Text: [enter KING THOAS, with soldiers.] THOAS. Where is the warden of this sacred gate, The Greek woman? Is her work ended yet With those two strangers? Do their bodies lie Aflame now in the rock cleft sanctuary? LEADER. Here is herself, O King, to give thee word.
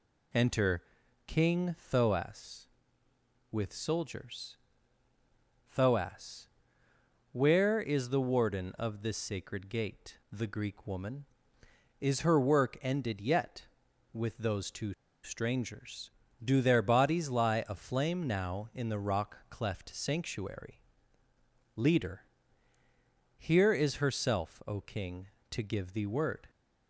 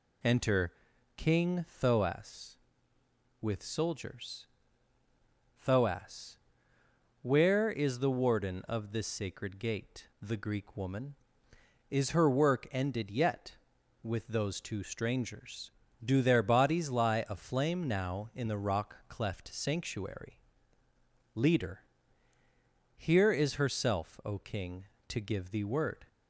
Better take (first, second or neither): second